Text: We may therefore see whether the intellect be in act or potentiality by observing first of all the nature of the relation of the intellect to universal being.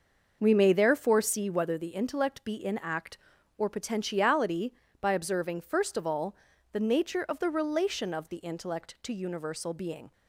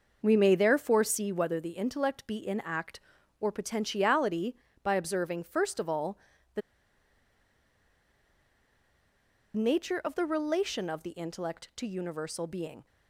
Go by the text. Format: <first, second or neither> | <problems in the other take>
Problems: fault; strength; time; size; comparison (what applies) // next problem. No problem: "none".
first | pauses between "all" and "the"; at 6.1 s; 0.38 s long; also in the first // pauses between "the" and "nature"; strong; at 6.6 s; 2.9 s long